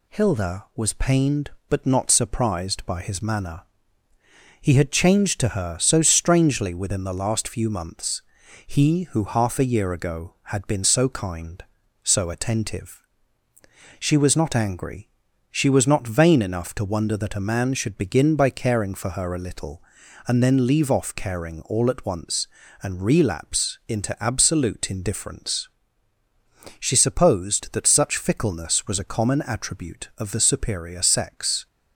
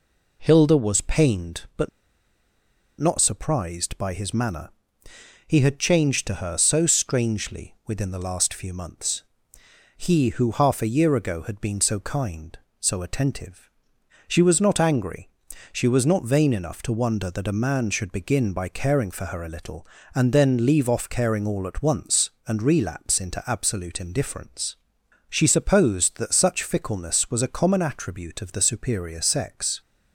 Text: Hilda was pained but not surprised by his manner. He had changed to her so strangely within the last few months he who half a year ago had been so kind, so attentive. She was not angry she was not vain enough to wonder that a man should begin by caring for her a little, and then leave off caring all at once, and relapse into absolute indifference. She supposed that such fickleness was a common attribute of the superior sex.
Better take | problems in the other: first | pauses between "but" and "not"; at 1.8 s; 1.1 s long // pauses between "months" and "he"; noticeable; at 9.2 s; 0.78 s long; also in the first // pauses between "angry" and "she"; at 15.2 s; 0.44 s long; also in the first

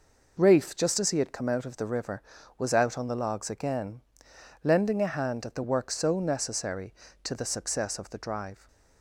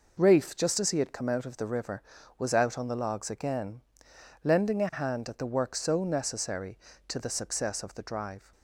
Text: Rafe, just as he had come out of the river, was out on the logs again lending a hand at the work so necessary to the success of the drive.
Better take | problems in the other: neither | pauses between "again" and "lending"; noticeable; the same in both

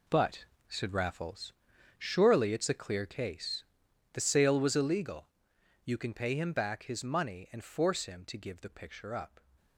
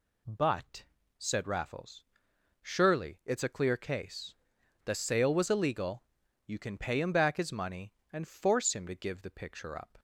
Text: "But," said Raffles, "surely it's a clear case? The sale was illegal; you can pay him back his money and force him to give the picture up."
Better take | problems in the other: second | gets quieter; strong; throughout; 11 dB

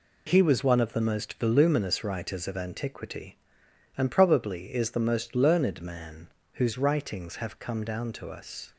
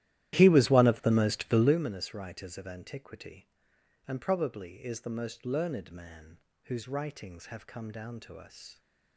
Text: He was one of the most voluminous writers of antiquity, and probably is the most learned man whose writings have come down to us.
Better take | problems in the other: first | starts louder than the rest; strong; until 1.8 s; 13.5 dB // pauses between "man" and "whose"; slight; at 6.3 s; 0.28 s long; slight in the first

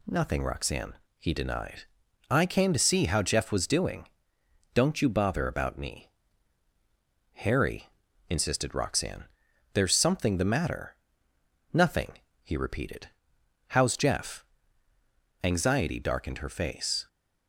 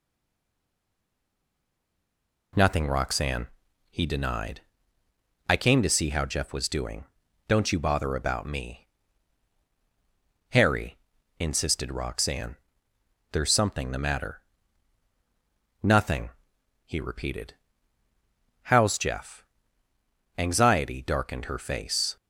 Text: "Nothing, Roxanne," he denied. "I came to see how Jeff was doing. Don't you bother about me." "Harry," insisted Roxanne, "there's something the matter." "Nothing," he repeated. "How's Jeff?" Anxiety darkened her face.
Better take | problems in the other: first | stays silent before the first word; until 2.5 s; 2.5 s long

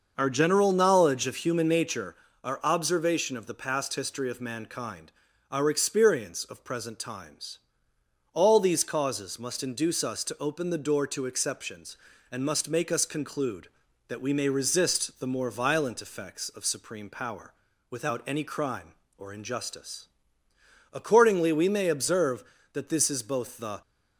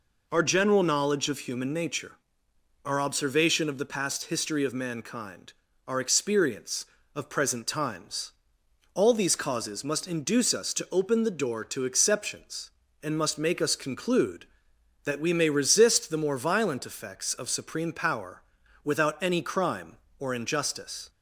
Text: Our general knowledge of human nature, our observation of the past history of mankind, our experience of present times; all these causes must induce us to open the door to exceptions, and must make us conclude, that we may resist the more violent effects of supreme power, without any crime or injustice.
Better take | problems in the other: second | starts louder than the rest; noticeable; until 1.1 s; 6 dB // goes on to say "Accordingly we may observe that this is both the"; strong; from 20.9 s on; 2.8 s long

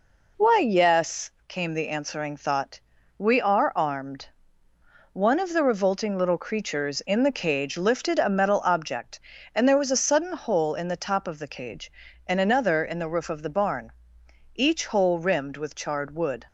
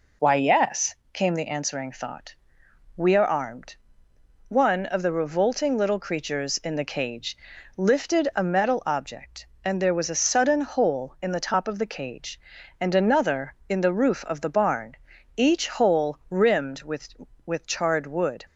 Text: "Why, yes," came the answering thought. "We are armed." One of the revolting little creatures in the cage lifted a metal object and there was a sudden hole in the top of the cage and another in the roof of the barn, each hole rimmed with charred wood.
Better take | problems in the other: first | pauses between "cage" and "lifted"; at 7.3 s; 0.40 s long // says "with" twice; at 17.4 s

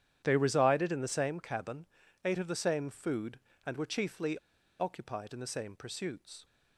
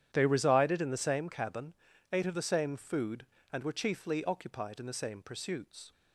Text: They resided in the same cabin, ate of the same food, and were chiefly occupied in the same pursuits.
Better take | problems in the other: second | starts louder than the rest; strong; until 1.2 s; 10 dB; strong in the second // pauses between "chiefly" and "occupied"; at 4.3 s; 0.41 s long

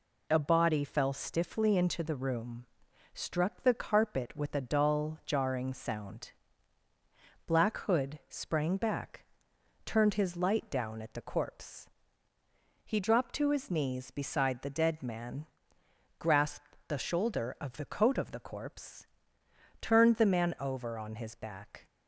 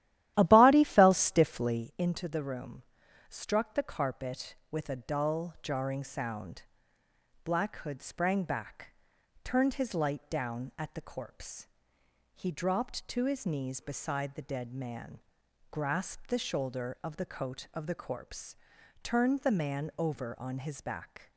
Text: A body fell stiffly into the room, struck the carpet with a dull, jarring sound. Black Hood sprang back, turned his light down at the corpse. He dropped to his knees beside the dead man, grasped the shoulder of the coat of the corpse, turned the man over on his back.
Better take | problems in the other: first | starts louder than the rest; strong; until 1.9 s; 13 dB

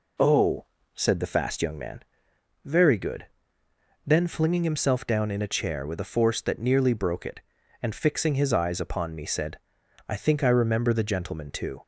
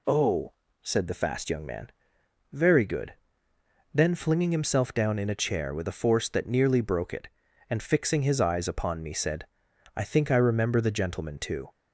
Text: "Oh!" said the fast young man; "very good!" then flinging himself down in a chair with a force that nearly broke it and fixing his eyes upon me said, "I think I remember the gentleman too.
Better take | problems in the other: second | starts louder than the rest; until 1.9 s; 3.5 dB

